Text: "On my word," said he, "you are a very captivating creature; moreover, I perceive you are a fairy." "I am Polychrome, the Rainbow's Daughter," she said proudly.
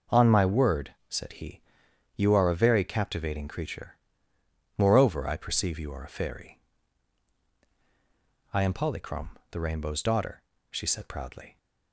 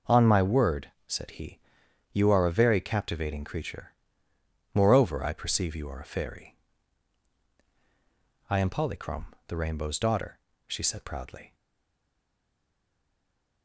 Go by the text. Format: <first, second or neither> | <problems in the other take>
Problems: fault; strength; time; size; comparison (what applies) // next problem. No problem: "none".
first | stays silent after the last word; from 11.5 s on; 2.1 s long